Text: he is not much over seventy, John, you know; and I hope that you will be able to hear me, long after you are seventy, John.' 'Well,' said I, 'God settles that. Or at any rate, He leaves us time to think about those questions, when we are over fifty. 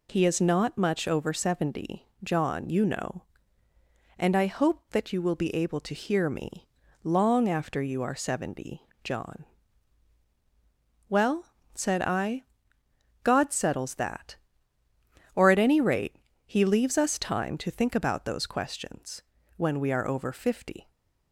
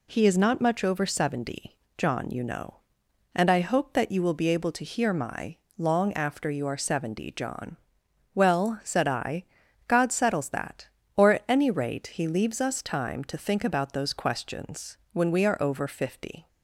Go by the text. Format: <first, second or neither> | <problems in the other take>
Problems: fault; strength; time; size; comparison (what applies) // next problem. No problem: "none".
first | says "my" for "me"; at 5.1 s